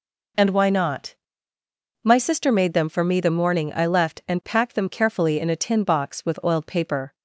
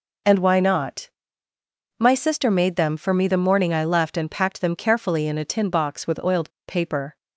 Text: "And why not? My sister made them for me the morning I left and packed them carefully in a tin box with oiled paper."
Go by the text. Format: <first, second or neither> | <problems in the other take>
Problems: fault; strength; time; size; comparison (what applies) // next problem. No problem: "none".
first | pauses between "oiled" and "paper"; slight; at 6.4 s; 0.17 s long